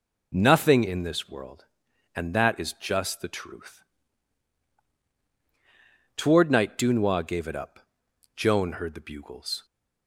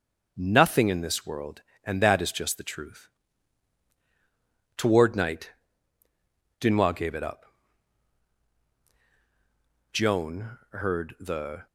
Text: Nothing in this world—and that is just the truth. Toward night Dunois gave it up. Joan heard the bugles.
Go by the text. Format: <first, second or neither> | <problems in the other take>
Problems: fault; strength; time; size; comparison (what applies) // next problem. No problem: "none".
first | starts louder than the rest; noticeable; until 1.3 s; 6 dB // pauses between "night" and "Dunois"; at 5.5 s; 1.1 s long // stops before "bugles"; at 11.6 s